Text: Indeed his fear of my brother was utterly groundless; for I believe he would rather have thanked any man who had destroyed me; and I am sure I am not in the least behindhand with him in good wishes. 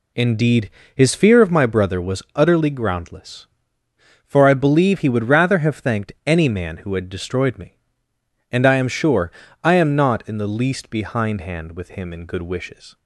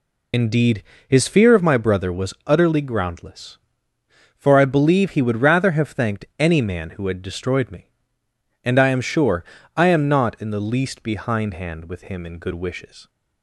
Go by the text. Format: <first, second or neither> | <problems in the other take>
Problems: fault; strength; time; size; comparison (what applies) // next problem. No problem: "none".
first | loses the start of "Indeed"; at 0.3 s; 55 ms // pauses between "Indeed" and "his"; slight; at 0.8 s; 0.26 s long; slight in the first // pauses between "sure" and "I"; slight; at 9.4 s; 0.32 s long; slight in the first